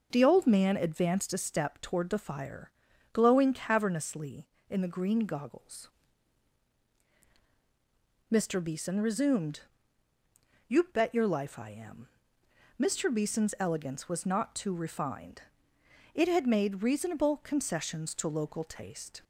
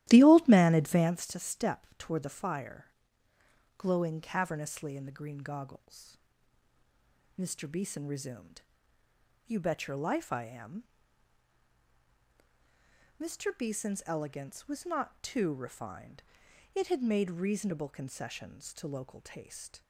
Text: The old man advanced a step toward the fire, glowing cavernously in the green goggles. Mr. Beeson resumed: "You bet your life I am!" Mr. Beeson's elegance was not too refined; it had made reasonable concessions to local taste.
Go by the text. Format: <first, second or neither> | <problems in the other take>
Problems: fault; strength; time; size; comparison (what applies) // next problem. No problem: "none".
first | starts louder than the rest; strong; until 1.3 s; 14 dB